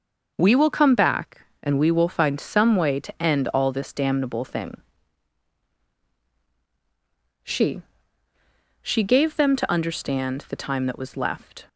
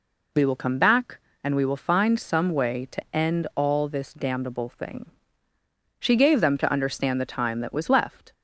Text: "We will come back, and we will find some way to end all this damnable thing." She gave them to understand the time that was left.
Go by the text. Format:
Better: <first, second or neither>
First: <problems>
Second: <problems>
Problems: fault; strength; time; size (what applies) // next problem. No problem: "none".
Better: second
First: says "She" twice; at 8.8 s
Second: none